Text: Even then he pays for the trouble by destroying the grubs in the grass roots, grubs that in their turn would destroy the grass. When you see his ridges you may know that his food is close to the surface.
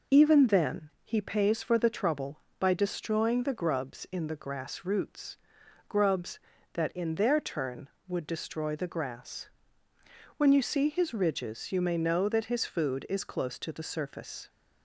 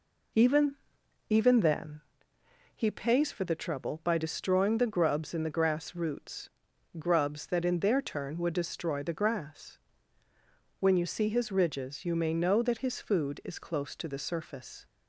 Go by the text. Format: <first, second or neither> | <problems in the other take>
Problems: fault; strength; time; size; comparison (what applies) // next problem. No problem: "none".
first | says "Even" twice; at 1.2 s // pauses between "then" and "he"; noticeable; at 2.0 s; 0.74 s long